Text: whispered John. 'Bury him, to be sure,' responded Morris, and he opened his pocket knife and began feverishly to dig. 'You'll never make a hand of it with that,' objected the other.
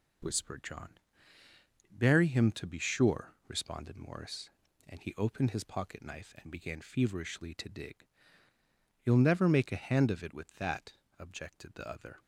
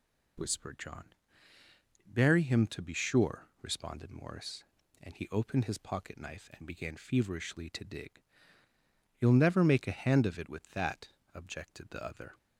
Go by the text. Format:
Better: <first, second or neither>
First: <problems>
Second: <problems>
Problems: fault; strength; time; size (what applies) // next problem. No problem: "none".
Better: second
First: gets quieter; noticeable; throughout; 5.5 dB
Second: none